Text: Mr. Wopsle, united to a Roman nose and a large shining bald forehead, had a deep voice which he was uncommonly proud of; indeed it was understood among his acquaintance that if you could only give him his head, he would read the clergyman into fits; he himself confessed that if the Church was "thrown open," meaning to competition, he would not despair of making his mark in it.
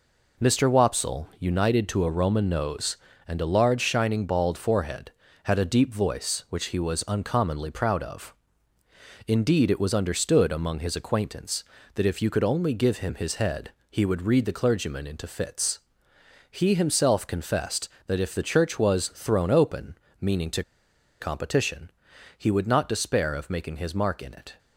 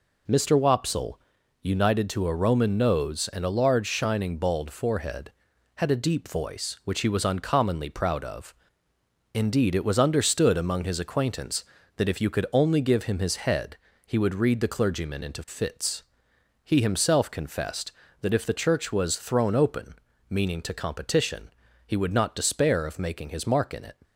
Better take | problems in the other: second | pauses between "to" and "competition"; noticeable; at 20.6 s; 0.59 s long

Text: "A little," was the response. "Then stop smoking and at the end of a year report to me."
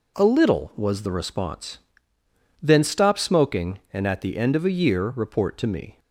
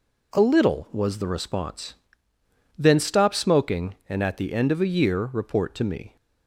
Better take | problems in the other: neither | none

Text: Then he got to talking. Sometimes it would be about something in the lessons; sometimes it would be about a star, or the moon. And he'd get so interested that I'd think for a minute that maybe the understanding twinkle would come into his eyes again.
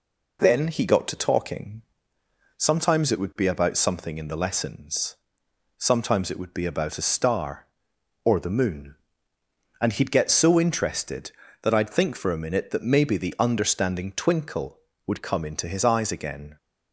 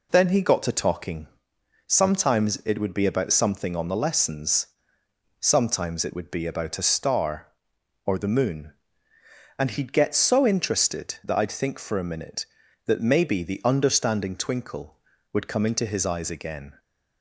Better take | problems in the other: first | says "on" for "in"; at 3.7 s

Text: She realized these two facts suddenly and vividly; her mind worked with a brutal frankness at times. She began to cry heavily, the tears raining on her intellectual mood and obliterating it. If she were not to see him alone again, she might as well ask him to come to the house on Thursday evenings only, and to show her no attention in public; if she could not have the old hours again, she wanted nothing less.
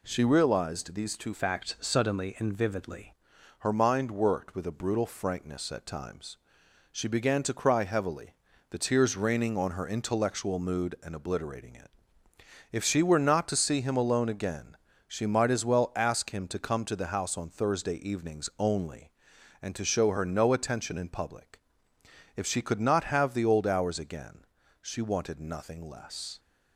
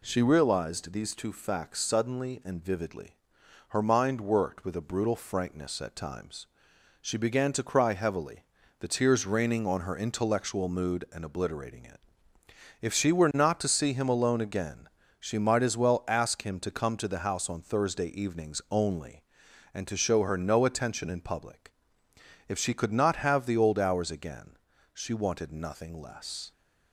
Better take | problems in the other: second | changes voice from "facts" to "vividly"; from 1.3 to 3.1 s; 1.8 s long

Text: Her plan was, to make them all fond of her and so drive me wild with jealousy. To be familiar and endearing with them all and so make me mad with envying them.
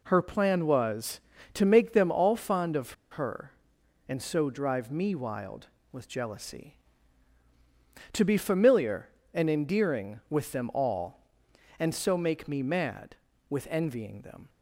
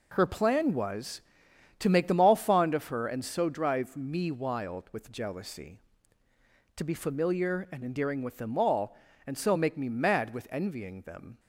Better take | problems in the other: second | pauses between "of" and "her"; slight; at 2.9 s; 0.20 s long

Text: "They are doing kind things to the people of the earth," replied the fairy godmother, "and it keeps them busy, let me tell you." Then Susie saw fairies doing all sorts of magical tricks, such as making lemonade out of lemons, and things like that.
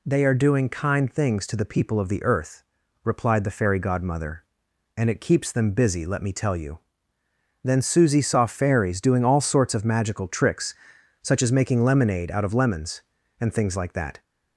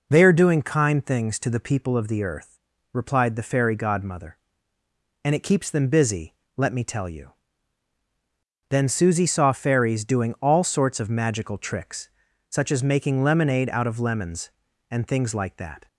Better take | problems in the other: neither | none

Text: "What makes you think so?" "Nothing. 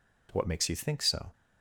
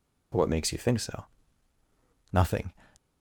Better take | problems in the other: second | stops before "Nothing"; at 1.3 s

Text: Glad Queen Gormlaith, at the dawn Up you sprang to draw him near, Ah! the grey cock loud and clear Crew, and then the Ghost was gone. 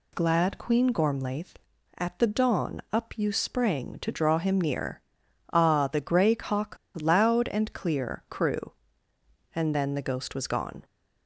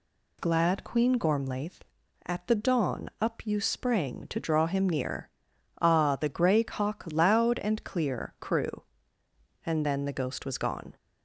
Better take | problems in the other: second | pauses between "cock" and "loud"; slight; at 6.7 s; 0.25 s long

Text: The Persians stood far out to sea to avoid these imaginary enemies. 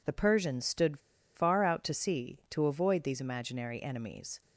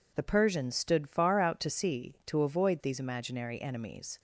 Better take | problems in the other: second | pauses between "stood" and "far"; slight; at 0.9 s; 0.36 s long

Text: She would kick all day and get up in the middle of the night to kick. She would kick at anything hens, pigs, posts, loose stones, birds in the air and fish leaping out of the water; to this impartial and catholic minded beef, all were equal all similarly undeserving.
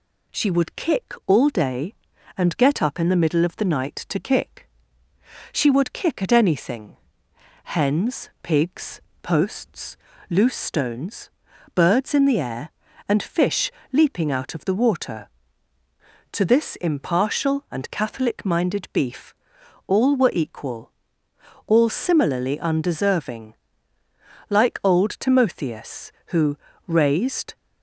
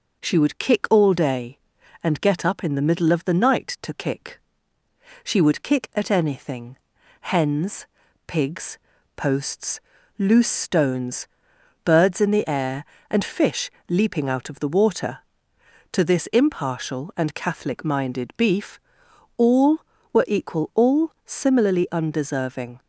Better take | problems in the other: second | pauses between "anything" and "hens"; noticeable; at 6.9 s; 0.68 s long; also in the second // pauses between "fish" and "leaping"; slight; at 13.7 s; 0.20 s long; slight in the second // pauses between "equal" and "all"; noticeable; at 20.9 s; 0.74 s long // goes on to say "Like old Timotheus who raised"; strong; from 24.4 s on; 3.0 s long

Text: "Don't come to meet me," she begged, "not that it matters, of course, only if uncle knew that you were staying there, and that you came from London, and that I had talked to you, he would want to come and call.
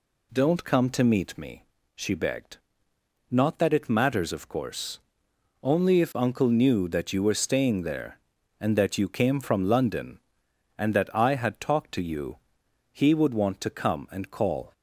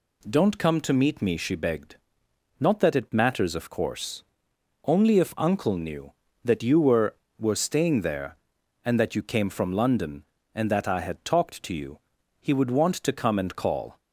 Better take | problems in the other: first | says "were" twice; at 7.3 s

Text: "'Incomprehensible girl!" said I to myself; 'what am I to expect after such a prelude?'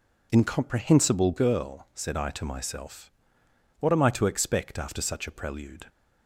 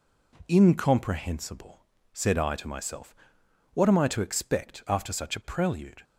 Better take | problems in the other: first | skips "girl"; at 1.9 s

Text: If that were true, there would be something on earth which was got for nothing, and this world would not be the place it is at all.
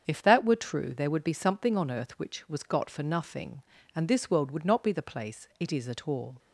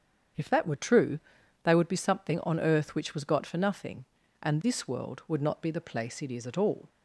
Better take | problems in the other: first | starts louder than the rest; strong; until 1.8 s; 8 dB; strong in the first // says "they" for "there"; at 1.6 s

